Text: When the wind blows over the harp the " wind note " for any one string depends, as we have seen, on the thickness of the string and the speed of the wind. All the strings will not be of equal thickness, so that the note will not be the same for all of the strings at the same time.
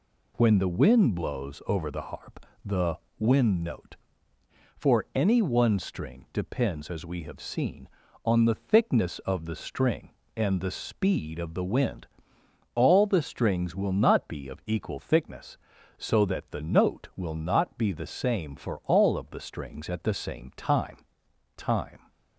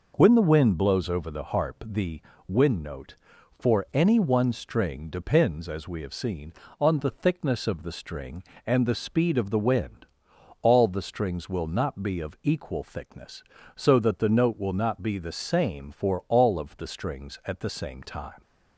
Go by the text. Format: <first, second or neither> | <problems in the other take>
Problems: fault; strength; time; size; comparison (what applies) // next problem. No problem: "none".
second | pauses between "harp" and "the"; slight; at 2.4 s; 0.20 s long // says "time" twice; at 21.5 s